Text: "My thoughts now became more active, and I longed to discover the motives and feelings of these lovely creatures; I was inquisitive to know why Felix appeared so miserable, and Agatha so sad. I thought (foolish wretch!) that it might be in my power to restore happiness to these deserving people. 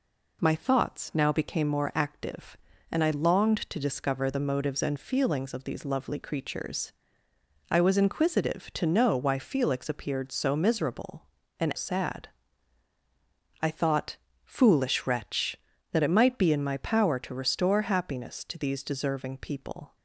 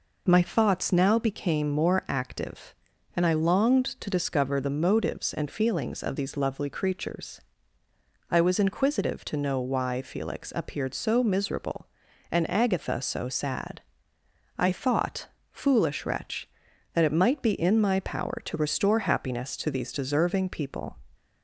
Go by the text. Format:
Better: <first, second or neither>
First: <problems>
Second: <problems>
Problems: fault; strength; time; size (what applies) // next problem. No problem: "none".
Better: second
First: skips "Agatha so"; at 11.7 s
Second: none